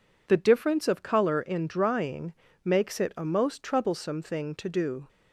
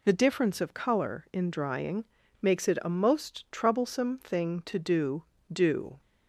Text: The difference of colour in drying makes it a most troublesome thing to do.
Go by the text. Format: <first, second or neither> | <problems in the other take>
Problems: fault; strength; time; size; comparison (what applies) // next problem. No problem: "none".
first | pauses between "drying" and "makes"; slight; at 2.0 s; 0.36 s long; slight in the first // says "do" twice; at 5.5 s